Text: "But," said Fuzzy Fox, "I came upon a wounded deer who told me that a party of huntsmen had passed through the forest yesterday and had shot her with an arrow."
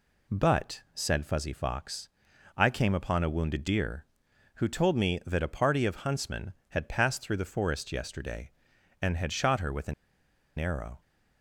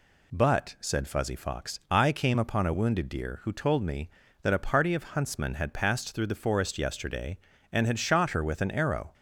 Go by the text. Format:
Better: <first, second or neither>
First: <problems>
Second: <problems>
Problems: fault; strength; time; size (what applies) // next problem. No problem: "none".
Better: second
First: pauses between "an" and "arrow"; noticeable; at 9.9 s; 0.64 s long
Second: none